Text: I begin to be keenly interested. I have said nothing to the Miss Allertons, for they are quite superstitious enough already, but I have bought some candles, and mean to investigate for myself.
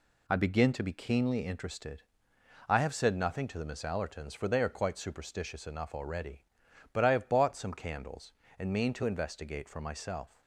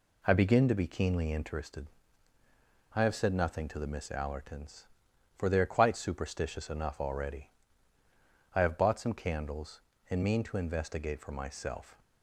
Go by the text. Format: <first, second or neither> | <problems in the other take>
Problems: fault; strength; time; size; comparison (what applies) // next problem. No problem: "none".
first | skips "but"; at 8.0 s